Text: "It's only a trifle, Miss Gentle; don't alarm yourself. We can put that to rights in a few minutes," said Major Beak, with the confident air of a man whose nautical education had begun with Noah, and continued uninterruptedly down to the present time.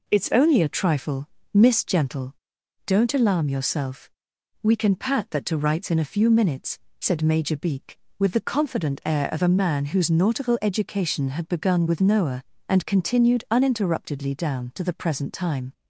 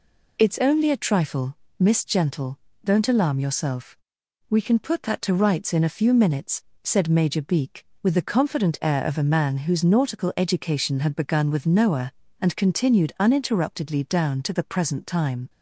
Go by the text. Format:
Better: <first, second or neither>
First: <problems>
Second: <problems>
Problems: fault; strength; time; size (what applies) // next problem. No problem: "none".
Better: second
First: says "pat" for "put"; at 4.9 s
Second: none